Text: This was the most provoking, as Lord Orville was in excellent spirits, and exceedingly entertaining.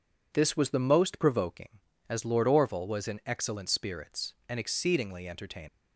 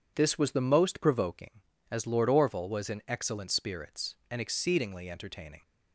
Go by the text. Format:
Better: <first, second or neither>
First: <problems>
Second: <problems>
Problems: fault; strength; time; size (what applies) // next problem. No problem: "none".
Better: second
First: leaves "entertaining" unfinished; at 5.6 s; 115 ms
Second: none